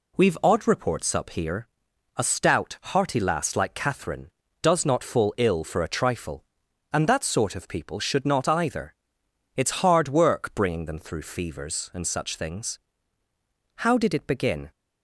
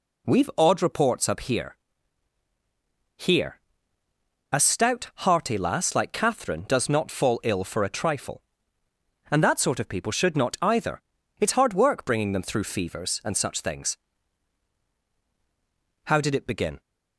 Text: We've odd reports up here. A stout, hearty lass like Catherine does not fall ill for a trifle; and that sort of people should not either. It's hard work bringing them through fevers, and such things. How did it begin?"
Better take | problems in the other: first | says "here" twice; at 3.1 s

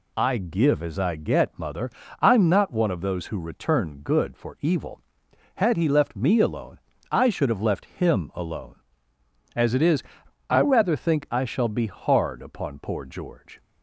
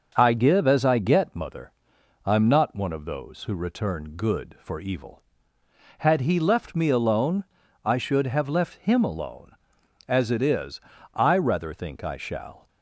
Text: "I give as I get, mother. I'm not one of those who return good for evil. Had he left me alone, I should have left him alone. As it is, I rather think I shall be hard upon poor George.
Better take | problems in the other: first | starts louder than the rest; until 1.1 s; 6 dB // stops before "be hard upon poor George"; at 12.6 s

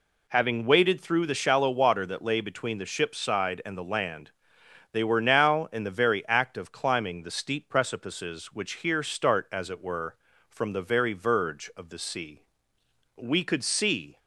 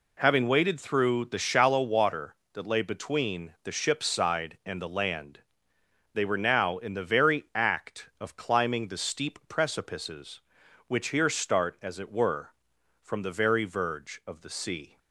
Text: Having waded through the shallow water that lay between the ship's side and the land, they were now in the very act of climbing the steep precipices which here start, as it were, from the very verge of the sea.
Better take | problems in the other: second | goes on to say "We could see"; noticeable; from 13.1 s on; 1.0 s long

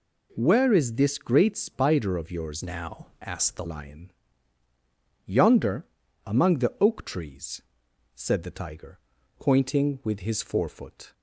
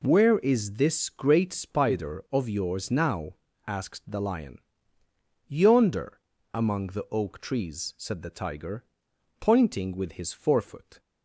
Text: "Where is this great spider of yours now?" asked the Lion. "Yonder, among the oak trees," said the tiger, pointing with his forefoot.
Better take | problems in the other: second | changes voice from "now" to "the"; from 2.6 to 3.6 s; 1.0 s long

